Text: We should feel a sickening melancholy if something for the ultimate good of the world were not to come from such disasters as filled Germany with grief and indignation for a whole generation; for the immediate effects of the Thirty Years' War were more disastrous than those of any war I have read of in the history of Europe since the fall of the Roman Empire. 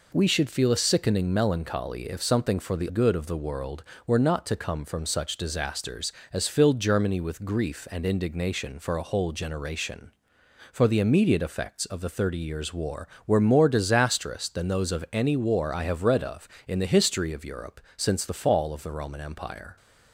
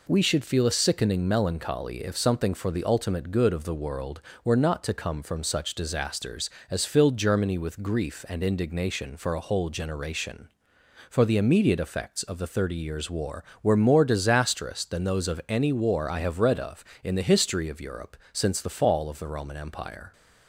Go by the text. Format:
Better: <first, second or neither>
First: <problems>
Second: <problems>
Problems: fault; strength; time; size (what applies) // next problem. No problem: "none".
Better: second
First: skips "ultimate"; at 2.9 s // pauses between "Europe" and "since"; slight; at 17.7 s; 0.16 s long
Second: pauses between "Europe" and "since"; slight; at 18.1 s; 0.16 s long